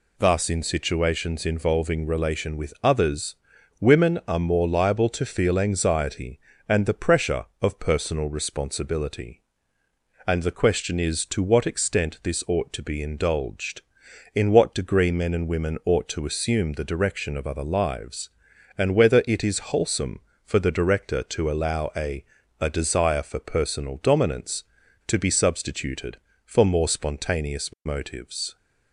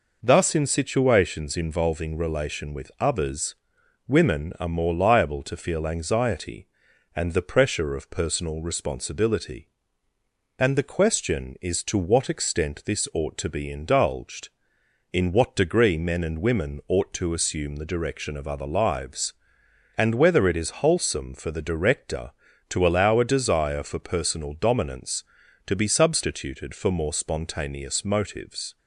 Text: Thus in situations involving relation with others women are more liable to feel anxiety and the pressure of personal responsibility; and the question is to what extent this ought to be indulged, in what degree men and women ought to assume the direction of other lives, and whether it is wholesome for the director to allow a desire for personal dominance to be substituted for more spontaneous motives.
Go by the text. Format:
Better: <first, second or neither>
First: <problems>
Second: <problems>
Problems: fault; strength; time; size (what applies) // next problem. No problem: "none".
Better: second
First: pauses between "others" and "women"; at 3.3 s; 0.44 s long // says "a" twice; at 22.6 s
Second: pauses between "others" and "women"; noticeable; at 3.5 s; 0.52 s long